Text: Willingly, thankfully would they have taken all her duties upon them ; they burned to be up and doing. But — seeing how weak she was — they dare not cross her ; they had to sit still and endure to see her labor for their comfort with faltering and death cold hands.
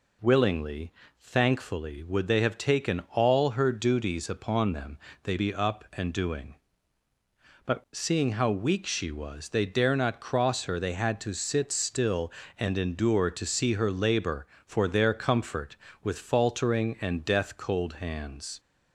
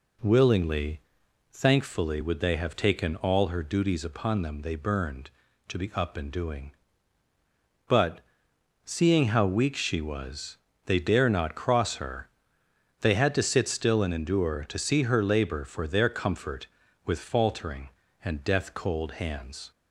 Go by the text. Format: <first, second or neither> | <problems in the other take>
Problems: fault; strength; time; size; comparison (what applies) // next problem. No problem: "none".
second | skips "burned to"; at 5.3 s